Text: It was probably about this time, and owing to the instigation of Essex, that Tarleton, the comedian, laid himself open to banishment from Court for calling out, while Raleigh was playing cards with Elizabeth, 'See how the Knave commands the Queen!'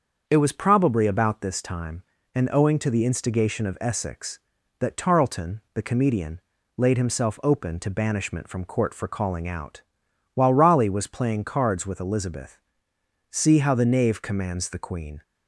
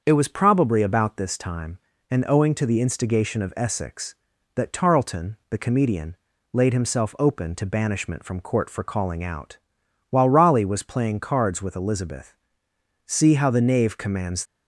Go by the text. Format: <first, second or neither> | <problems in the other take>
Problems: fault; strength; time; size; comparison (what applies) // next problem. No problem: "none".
first | starts louder than the rest; until 1.0 s; 7 dB; also in the first // stops before "the Queen"; at 14.4 s